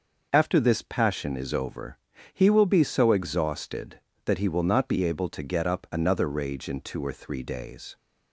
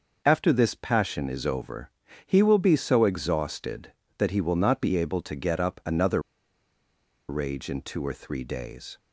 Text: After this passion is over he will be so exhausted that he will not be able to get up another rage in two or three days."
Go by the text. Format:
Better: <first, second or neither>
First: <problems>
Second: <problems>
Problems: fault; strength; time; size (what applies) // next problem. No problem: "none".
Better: first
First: starts louder than the rest; noticeable; until 1.3 s; 6 dB // pauses between "over" and "he"; slight; at 1.9 s; 0.36 s long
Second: starts louder than the rest; noticeable; until 1.2 s; 6 dB // pauses between "over" and "he"; slight; at 1.9 s; 0.36 s long // pauses between "another" and "rage"; at 6.2 s; 1.0 s long